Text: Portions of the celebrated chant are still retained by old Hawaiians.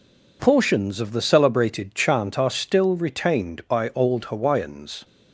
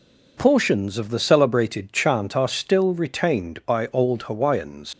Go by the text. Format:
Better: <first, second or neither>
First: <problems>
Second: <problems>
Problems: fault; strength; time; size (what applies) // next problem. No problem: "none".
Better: first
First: none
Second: leaves "Hawaiians" unfinished; at 4.9 s; 95 ms